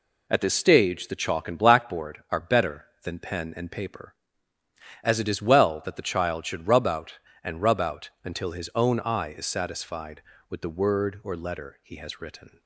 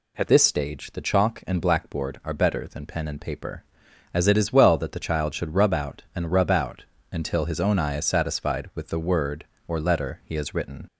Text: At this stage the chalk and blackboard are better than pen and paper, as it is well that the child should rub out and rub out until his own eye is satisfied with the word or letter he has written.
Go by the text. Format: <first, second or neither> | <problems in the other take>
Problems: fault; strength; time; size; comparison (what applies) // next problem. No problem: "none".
first | changes voice at "this"; from 0.2 s on; 10.6 s long // pauses between "out" and "until"; slight; at 6.8 s; 0.26 s long